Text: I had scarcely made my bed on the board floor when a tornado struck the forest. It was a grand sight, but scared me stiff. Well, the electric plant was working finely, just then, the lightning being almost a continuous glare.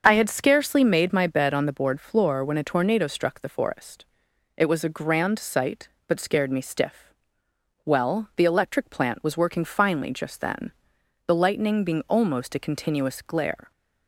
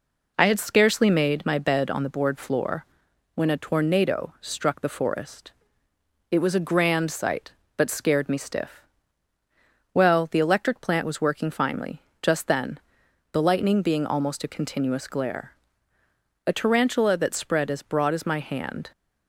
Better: first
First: none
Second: pauses between "floor" and "when"; noticeable; at 2.8 s; 0.50 s long // goes on to say "A tarantula that spread as broad as my hand"; strong; from 16.4 s on; 2.4 s long

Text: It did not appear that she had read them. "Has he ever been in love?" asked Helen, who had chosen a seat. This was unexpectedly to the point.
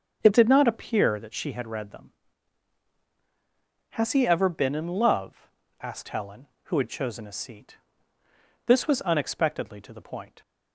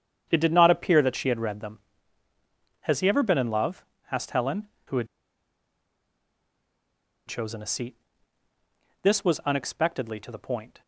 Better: first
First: starts louder than the rest; until 1.2 s; 6.5 dB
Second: starts louder than the rest; strong; until 1.3 s; 8.5 dB // pauses between "had" and "chosen"; strong; at 5.0 s; 2.2 s long

